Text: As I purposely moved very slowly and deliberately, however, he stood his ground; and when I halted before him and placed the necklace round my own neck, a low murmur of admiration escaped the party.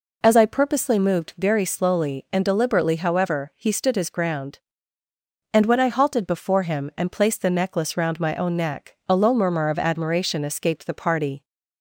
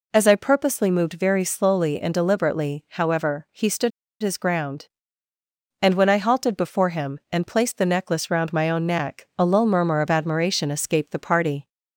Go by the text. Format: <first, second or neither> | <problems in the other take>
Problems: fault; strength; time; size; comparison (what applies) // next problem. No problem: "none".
first | pauses between "stood" and "his"; slight; at 3.9 s; 0.31 s long